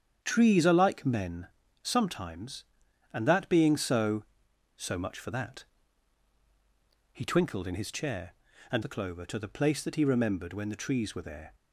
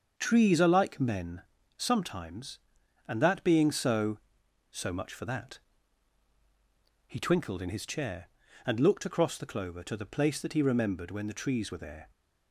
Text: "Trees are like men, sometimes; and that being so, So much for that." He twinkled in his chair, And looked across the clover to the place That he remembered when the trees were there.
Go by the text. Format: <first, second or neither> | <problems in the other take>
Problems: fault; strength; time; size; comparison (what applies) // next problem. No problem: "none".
second | starts louder than the rest; strong; until 1.2 s; 8 dB; also in the second // skips "looked across"; at 8.8 s